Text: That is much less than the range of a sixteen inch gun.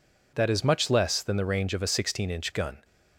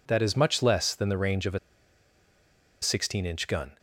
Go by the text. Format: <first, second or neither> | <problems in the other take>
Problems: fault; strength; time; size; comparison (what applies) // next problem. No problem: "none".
first | pauses between "a" and "sixteen"; at 1.5 s; 1.2 s long